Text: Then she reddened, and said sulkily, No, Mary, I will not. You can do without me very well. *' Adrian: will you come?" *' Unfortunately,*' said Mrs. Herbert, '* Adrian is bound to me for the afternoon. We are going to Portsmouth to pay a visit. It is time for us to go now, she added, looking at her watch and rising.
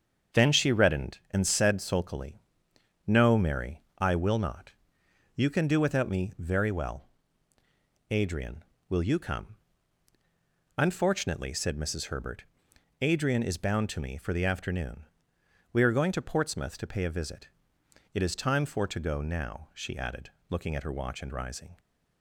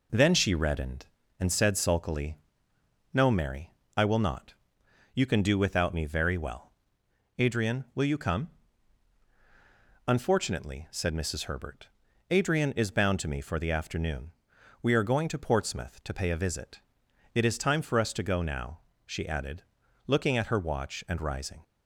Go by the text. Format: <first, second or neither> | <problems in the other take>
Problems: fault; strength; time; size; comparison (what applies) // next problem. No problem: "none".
second | starts louder than the rest; strong; until 1.4 s; 7.5 dB // skips "us"; at 18.8 s